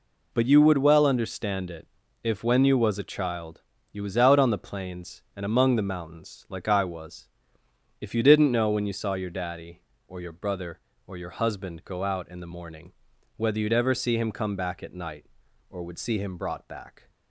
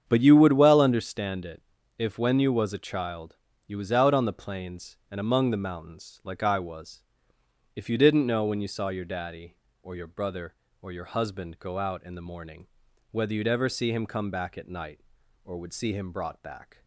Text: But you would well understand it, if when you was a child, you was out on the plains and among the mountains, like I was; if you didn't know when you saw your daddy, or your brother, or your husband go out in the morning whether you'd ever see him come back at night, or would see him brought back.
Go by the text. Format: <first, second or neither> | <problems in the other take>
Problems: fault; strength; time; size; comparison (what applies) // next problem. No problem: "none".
first | starts louder than the rest; strong; until 1.1 s; 8 dB // pauses between "morning" and "whether"; at 12.6 s; 0.42 s long; also in the first